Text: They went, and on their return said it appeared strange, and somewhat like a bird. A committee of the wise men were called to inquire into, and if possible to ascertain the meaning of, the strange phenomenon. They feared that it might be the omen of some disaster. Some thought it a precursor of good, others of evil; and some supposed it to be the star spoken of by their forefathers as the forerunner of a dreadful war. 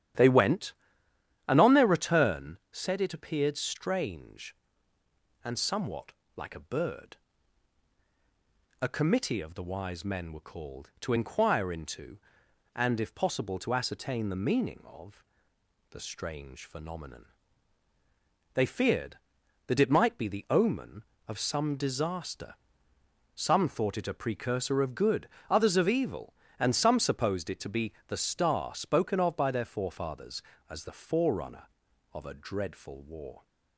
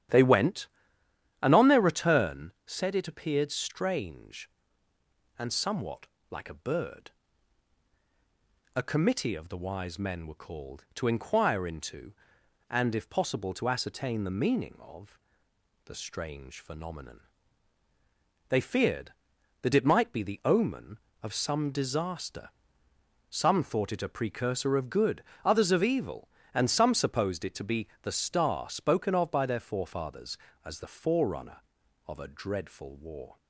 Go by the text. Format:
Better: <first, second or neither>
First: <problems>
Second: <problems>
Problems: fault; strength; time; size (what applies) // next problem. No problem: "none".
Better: neither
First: starts louder than the rest; strong; until 1.9 s; 11 dB // pauses between "somewhat" and "like"; slight; at 6.1 s; 0.24 s long // pauses between "be" and "the"; slight; at 27.9 s; 0.16 s long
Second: starts louder than the rest; strong; until 1.8 s; 11 dB // pauses between "somewhat" and "like"; slight; at 6.0 s; 0.24 s long // pauses between "be" and "the"; slight; at 27.8 s; 0.16 s long